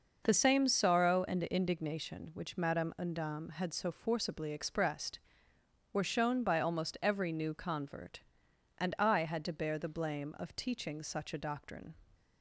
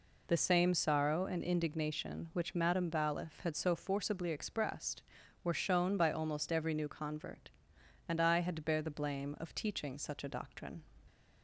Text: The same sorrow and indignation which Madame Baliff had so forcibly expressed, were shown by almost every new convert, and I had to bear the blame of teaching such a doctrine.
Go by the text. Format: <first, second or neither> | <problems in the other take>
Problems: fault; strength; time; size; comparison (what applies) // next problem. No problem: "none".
second | says "Undam" for "Baliff"; at 2.9 s